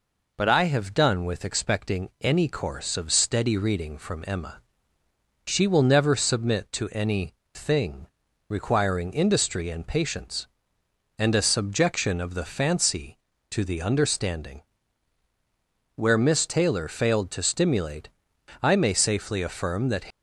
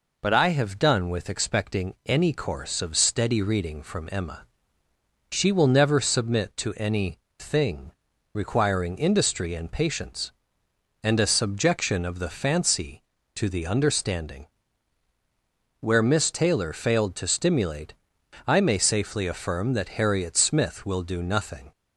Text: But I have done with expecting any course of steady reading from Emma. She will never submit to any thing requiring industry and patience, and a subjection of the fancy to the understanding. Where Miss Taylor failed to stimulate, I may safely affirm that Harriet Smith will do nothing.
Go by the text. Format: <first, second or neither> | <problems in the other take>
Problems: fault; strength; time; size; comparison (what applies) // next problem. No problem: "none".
second | pauses between "any" and "thing"; slight; at 7.3 s; 0.18 s long; slight in the second // pauses between "thing" and "requiring"; at 8.0 s; 0.42 s long; also in the second // stops before "Harriet Smith will do nothing"; at 20.1 s